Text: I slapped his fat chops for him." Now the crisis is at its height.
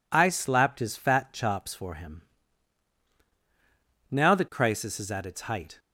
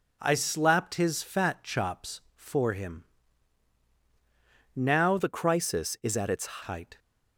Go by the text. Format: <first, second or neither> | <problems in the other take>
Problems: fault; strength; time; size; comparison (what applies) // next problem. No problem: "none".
first | changes voice from "the" to "its"; from 5.1 to 6.6 s; 1.5 s long